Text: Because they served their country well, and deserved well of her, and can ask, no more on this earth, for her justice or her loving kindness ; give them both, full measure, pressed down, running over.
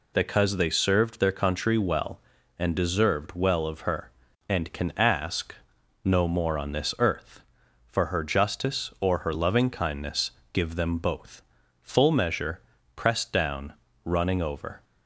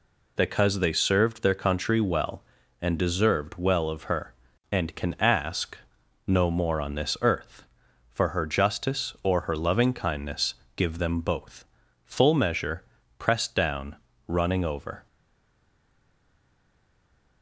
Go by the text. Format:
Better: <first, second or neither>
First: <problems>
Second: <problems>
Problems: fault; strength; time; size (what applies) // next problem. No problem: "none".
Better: first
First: none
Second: stays silent after the last word; from 15.0 s on; 2.4 s long